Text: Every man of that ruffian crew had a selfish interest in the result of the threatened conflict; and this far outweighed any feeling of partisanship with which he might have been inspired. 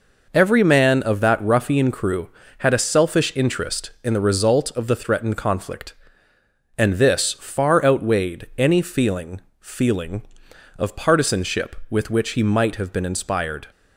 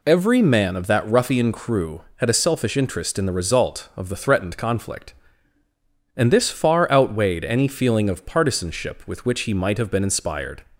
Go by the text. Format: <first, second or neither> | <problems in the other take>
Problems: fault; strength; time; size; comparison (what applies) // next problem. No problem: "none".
second | says "feeling" twice; at 9.5 s